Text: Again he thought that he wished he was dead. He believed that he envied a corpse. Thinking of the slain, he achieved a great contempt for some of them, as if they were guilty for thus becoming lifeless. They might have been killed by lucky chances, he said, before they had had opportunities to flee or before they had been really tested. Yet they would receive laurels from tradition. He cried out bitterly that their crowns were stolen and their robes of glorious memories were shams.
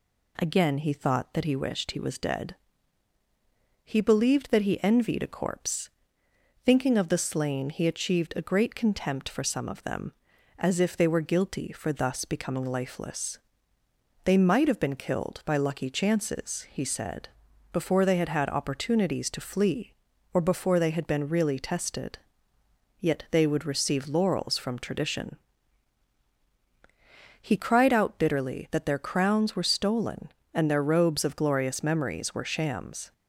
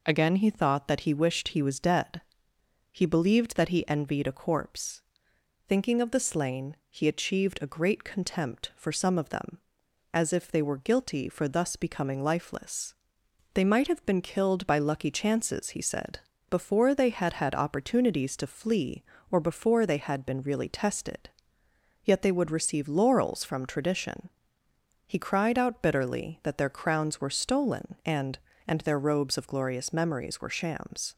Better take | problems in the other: first | says "and" twice; at 28.6 s

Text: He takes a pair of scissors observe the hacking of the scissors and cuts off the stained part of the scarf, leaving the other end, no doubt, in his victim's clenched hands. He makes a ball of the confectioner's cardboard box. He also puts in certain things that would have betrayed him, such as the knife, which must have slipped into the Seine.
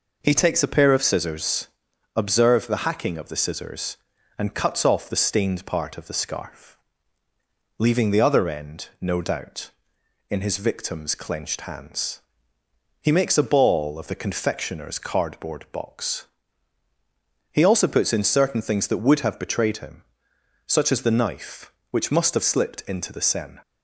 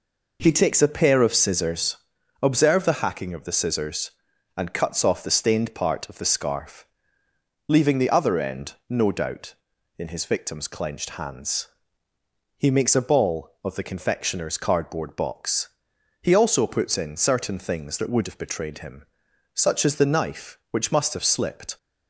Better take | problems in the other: first | pauses between "scissors" and "observe"; at 1.9 s; 0.44 s long; noticeable in the first // stops before "into the Seine"; at 21.7 s

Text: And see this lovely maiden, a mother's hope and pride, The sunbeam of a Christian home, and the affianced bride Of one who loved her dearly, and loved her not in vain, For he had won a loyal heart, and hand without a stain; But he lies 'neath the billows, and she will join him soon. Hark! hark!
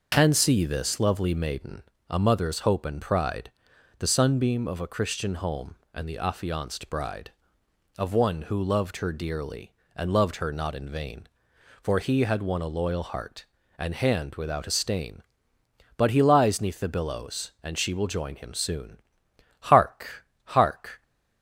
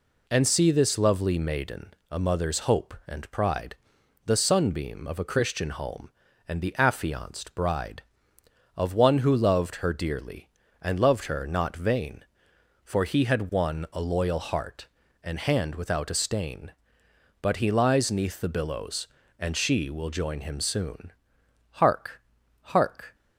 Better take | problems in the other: first | skips "in"; at 11.7 s

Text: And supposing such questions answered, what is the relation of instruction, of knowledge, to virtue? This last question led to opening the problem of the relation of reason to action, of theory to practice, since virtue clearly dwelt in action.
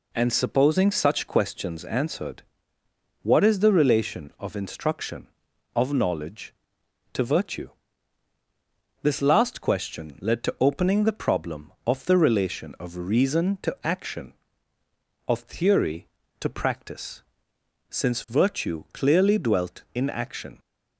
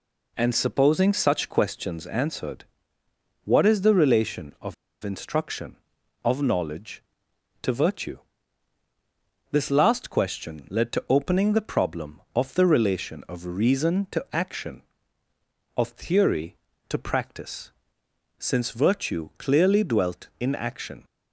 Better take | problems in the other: first | pauses between "of" and "instruction"; slight; at 4.7 s; 0.29 s long

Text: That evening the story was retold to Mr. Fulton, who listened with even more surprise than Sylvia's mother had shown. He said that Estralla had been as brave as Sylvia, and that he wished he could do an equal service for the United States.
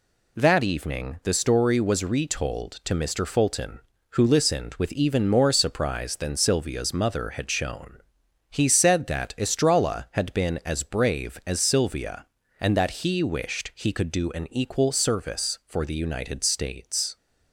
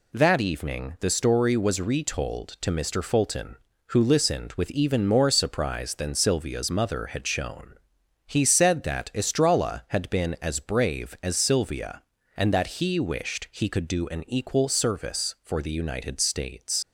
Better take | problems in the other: first | leaves "States" unfinished; at 16.8 s; 100 ms

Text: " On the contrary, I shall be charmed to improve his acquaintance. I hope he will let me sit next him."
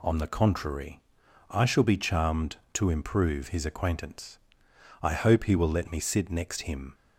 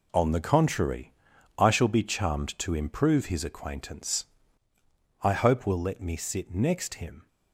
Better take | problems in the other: first | skips "he"; at 5.6 s

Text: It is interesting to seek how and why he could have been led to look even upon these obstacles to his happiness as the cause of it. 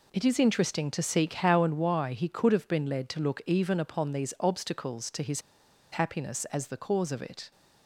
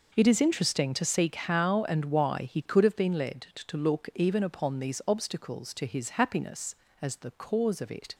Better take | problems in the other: second | pauses between "his" and "happiness"; noticeable; at 5.4 s; 0.51 s long

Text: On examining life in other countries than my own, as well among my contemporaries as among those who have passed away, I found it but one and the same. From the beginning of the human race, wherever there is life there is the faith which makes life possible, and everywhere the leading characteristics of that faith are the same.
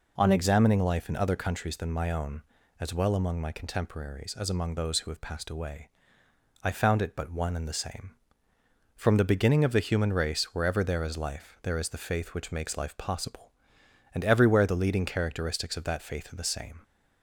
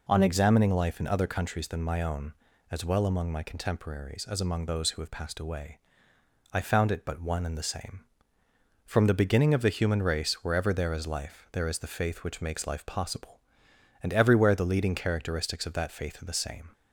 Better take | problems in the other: neither | none

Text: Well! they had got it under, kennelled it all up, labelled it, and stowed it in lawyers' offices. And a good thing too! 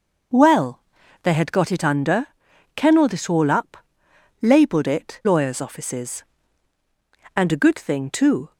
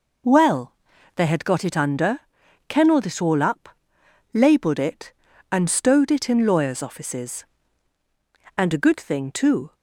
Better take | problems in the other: second | skips "and stowed it in"; at 5.2 s

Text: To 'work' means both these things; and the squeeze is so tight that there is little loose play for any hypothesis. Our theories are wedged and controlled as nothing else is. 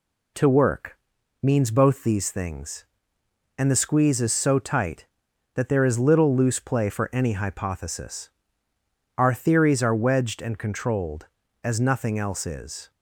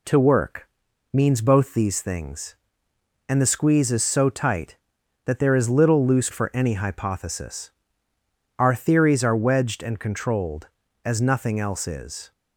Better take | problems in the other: first | pauses between "work" and "means"; at 0.6 s; 0.44 s long; also in the first // skips "play"; at 6.2 s

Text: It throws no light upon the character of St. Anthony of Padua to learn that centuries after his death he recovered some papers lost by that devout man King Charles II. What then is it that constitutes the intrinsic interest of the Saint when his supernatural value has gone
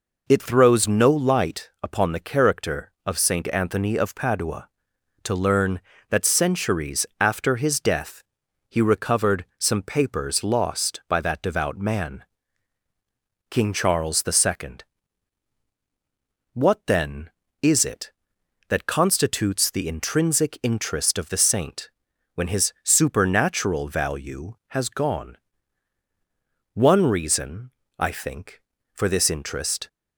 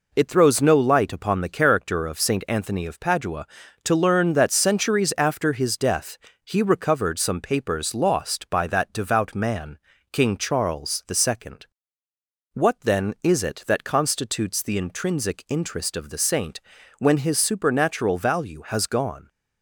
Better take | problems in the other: second | pauses between "death" and "he"; at 8.2 s; 0.44 s long; slight in the second // pauses between "man" and "King"; strong; at 12.2 s; 1.2 s long; slight in the second // pauses between "Saint" and "when"; at 21.8 s; 0.44 s long; also in the second // goes on to say "One reason I think for this interest"; strong; from 26.7 s on; 3.1 s long

